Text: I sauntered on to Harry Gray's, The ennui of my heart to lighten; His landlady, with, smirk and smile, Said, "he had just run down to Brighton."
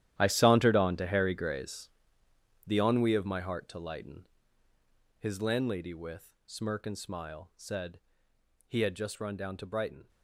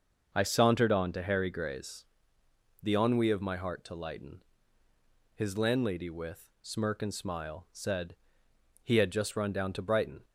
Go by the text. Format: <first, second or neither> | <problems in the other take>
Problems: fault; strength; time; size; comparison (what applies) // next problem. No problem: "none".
second | gets quieter; strong; throughout; 15.5 dB // starts louder than the rest; strong; until 1.1 s; 12 dB; also in the second